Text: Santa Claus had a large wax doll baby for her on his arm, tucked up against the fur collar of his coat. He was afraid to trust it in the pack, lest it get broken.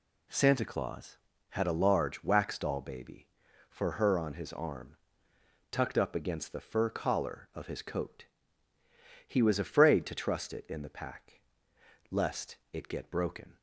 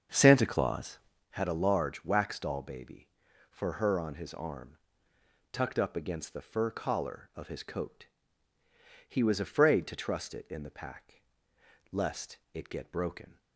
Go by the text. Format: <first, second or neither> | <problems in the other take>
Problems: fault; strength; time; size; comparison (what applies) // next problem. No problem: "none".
first | starts louder than the rest; until 1.3 s; 7 dB